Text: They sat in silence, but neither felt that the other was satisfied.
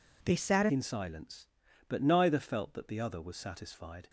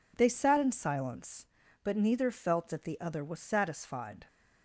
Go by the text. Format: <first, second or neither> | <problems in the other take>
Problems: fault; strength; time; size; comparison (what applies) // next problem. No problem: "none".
second | changes voice at "in"; from 0.7 s on; 3.3 s long